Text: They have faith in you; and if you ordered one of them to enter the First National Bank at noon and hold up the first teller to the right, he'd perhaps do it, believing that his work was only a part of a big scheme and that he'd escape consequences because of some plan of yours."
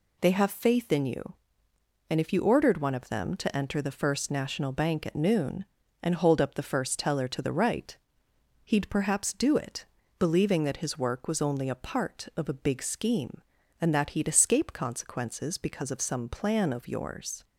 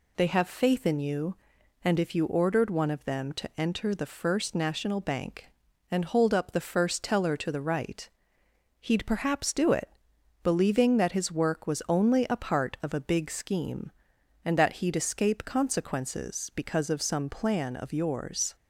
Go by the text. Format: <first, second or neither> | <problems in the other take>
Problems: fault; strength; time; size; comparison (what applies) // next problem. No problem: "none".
first | skips "at noon"; at 5.6 s